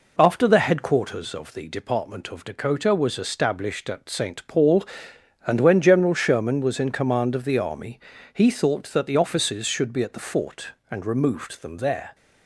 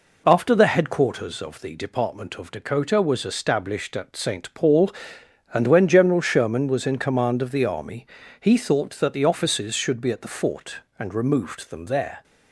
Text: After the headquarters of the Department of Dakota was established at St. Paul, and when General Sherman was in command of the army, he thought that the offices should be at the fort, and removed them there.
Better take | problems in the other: neither | none

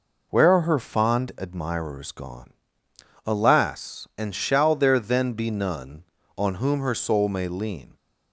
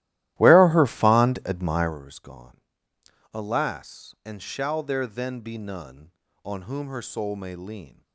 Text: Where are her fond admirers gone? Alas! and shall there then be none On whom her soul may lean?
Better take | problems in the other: first | starts louder than the rest; strong; until 2.0 s; 15 dB

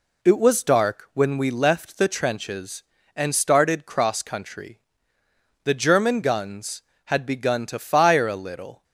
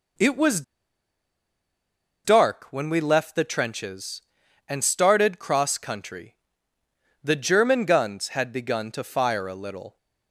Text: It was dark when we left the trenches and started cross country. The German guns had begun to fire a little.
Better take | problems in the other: first | pauses between "was" and "dark"; strong; at 0.6 s; 1.6 s long

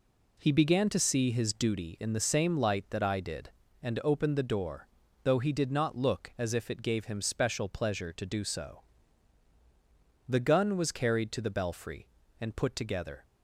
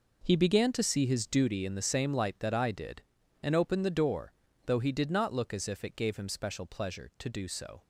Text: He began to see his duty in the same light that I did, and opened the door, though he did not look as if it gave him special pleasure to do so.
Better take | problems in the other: second | goes on to say "The gun was carried to the belfry and put together"; strong; from 10.2 s on; 2.9 s long

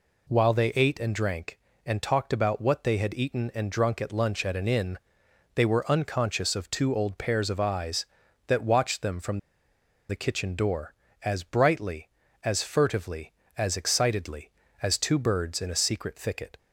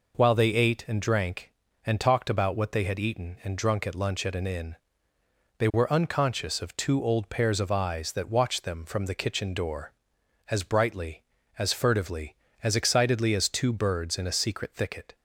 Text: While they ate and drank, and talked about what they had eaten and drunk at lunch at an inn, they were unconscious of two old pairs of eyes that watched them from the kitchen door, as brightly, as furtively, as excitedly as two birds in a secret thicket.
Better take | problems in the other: second | pauses between "from" and "the"; noticeable; at 9.3 s; 0.71 s long

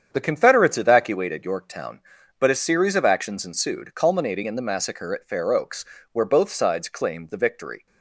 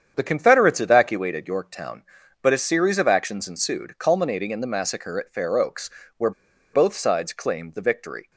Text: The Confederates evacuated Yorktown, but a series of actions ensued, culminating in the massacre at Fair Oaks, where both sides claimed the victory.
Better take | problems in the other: first | starts louder than the rest; strong; until 1.1 s; 8 dB; strong in the first // pauses between "where" and "both"; at 6.3 s; 0.42 s long

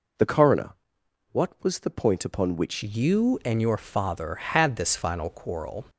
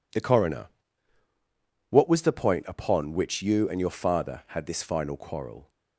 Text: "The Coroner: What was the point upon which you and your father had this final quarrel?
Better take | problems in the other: second | changes voice at "you"; from 2.8 s on; 3.0 s long

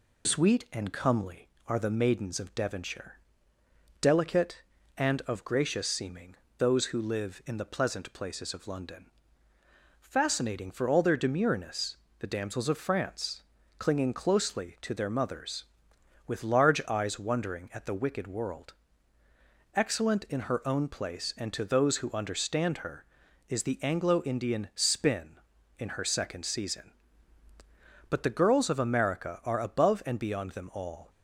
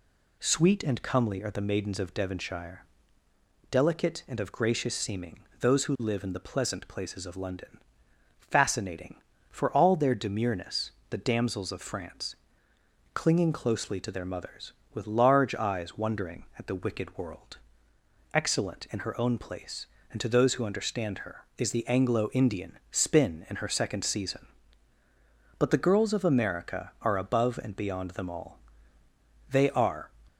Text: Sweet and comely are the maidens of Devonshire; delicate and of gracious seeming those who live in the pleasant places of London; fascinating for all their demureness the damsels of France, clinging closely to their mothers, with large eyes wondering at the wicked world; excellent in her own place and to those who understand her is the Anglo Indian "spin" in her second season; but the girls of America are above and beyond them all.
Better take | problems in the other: first | pauses between "seeming" and "those"; slight; at 5.3 s; 0.20 s long; slight in the first // pauses between "demureness" and "the"; slight; at 10.9 s; 0.18 s long; slight in the first // goes on to say "They are"; from 29.4 s on; 0.60 s long

